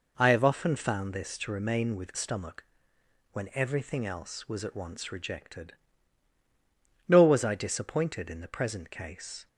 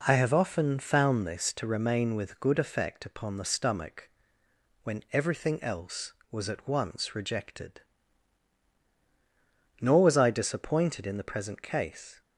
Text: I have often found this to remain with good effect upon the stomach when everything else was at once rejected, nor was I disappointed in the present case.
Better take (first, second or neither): second